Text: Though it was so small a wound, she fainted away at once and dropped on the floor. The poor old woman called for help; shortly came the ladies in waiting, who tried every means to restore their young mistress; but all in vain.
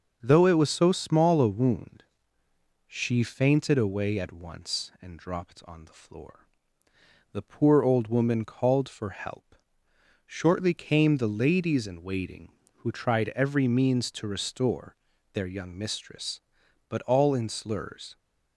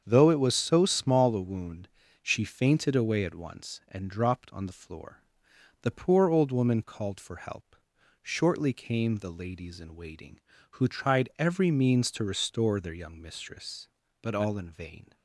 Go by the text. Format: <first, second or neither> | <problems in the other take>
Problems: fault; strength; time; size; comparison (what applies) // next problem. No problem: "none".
second | starts louder than the rest; until 1.2 s; 6 dB; strong in the second // pauses between "restore" and "their"; slight; at 14.9 s; 0.34 s long // says "slurs" for "vain"; at 17.4 s